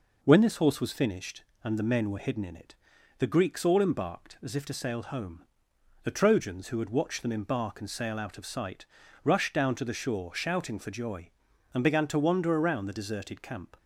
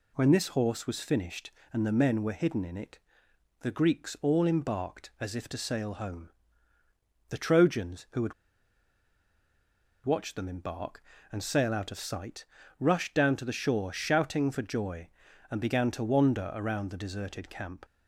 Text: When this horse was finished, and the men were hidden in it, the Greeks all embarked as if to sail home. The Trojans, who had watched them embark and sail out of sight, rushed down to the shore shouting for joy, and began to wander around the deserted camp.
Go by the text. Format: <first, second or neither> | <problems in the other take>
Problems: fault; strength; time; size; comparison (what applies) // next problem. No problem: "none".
first | pauses between "had" and "watched"; strong; at 8.3 s; 1.7 s long